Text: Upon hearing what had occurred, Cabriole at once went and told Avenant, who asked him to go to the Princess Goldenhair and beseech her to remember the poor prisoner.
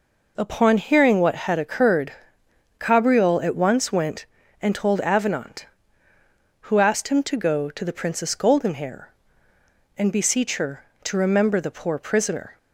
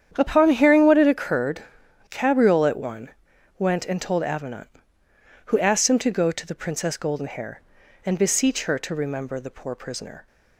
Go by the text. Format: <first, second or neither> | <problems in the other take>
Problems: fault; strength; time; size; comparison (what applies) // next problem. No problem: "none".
first | starts louder than the rest; strong; until 1.1 s; 8.5 dB // says "one" for "once"; at 2.7 s